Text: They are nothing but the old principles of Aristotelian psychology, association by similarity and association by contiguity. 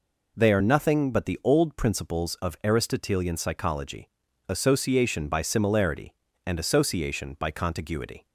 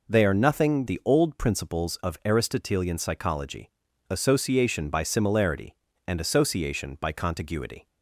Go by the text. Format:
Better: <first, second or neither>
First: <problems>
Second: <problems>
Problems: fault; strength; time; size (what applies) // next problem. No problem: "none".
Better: first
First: none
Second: skips "but"; at 0.8 s